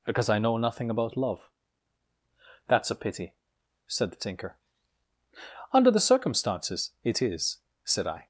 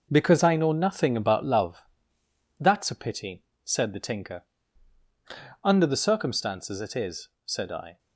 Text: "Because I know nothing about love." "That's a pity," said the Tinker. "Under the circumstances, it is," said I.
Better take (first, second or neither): first